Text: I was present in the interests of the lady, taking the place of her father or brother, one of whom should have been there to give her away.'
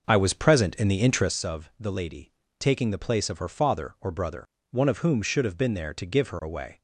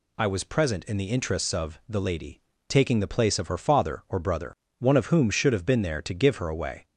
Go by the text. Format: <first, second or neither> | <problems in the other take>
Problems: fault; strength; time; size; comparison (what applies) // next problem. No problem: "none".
second | starts louder than the rest; noticeable; until 1.4 s; 6 dB